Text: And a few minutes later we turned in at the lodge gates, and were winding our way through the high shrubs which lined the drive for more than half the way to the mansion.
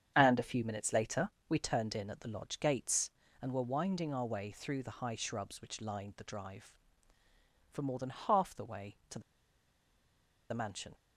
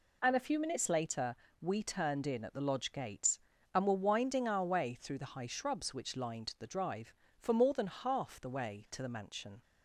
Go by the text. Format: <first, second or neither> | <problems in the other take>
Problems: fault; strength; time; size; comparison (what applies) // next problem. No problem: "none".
second | starts louder than the rest; strong; until 1.1 s; 8 dB // pauses between "later" and "we"; slight; at 1.3 s; 0.18 s long; slight in the second // pauses between "the" and "mansion"; strong; at 9.2 s; 1.3 s long